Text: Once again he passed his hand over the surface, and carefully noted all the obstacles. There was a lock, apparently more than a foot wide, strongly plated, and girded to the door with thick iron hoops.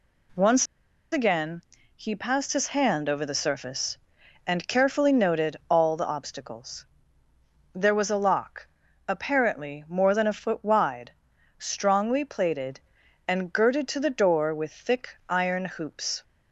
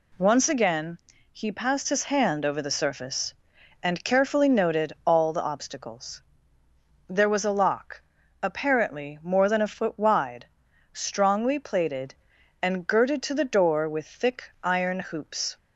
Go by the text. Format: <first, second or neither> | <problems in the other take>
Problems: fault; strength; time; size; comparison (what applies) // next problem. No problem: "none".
second | pauses between "Once" and "again"; noticeable; at 0.6 s; 0.47 s long // pauses between "again" and "he"; slight; at 1.5 s; 0.36 s long; slight in the second